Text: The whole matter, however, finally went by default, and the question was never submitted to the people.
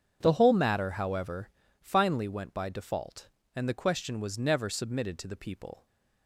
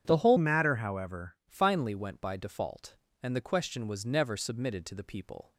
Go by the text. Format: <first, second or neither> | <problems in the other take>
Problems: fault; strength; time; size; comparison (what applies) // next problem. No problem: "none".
first | starts louder than the rest; strong; until 1.0 s; 8.5 dB; strong in the first // changes voice from "matter" to "however"; from 0.3 to 1.3 s; 1.0 s long